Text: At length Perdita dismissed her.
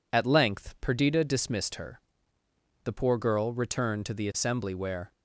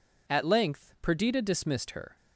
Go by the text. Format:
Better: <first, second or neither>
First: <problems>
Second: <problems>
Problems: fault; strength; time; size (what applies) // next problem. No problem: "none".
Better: second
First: goes on to say "The poor girl returned to the assembly where"; strong; from 2.8 s on; 2.2 s long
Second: none